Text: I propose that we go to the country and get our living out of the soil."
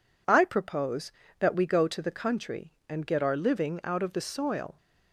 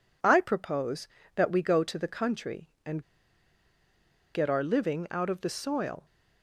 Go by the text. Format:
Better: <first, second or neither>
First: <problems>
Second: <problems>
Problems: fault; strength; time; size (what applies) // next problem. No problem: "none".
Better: first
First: none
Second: pauses between "and" and "get"; strong; at 3.0 s; 1.3 s long